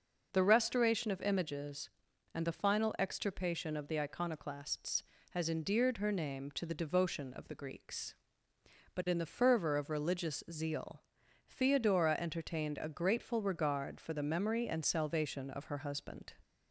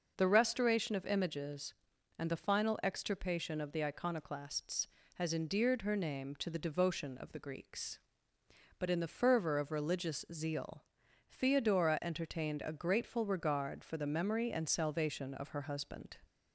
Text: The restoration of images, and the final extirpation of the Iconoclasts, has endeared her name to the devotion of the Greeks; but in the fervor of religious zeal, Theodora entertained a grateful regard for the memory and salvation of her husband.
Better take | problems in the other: neither | none

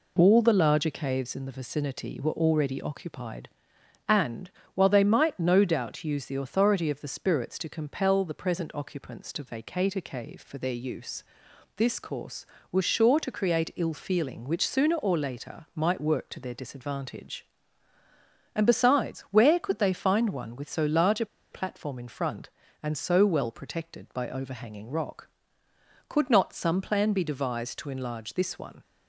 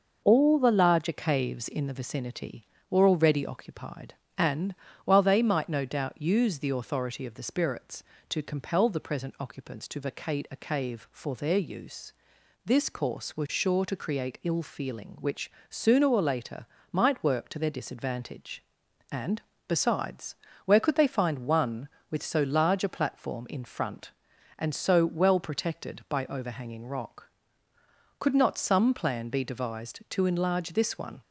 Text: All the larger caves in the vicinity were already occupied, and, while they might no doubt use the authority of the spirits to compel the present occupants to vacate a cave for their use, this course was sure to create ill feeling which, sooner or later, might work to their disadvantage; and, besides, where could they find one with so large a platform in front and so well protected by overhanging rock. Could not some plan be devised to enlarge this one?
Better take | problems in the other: second | pauses between "a" and "platform"; slight; at 21.2 s; 0.24 s long

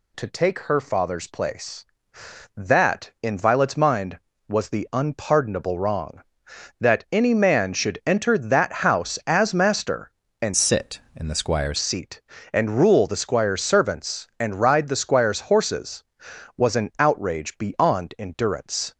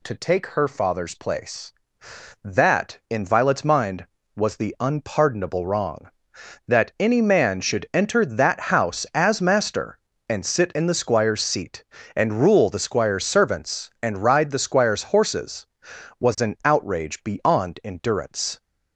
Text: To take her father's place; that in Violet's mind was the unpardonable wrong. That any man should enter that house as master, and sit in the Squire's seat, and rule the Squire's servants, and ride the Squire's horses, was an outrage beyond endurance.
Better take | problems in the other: second | changes voice from "sit" to "Squire's"; from 10.5 to 11.7 s; 1.2 s long

